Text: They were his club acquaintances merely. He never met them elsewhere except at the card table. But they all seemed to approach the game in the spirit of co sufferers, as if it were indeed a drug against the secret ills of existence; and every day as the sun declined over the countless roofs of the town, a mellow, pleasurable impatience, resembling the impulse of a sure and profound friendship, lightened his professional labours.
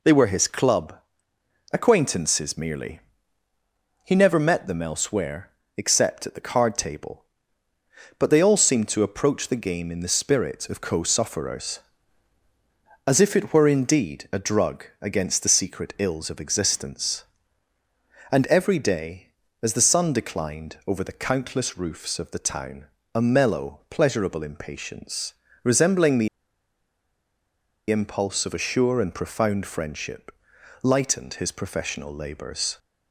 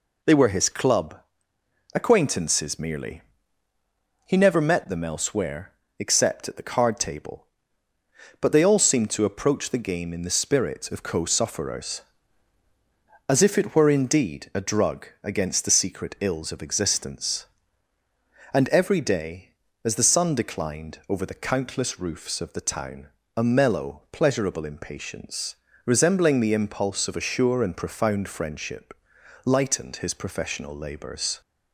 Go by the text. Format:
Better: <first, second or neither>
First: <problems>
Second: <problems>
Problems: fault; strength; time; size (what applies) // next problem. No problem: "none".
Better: second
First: pauses between "club" and "acquaintances"; noticeable; at 0.9 s; 0.78 s long // pauses between "elsewhere" and "except"; slight; at 5.5 s; 0.26 s long // pauses between "drug" and "against"; slight; at 14.8 s; 0.18 s long // pauses between "the" and "impulse"; strong; at 26.2 s; 1.6 s long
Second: pauses between "club" and "acquaintances"; noticeable; at 1.1 s; 0.78 s long // pauses between "elsewhere" and "except"; slight; at 5.7 s; 0.26 s long // pauses between "drug" and "against"; slight; at 15.0 s; 0.18 s long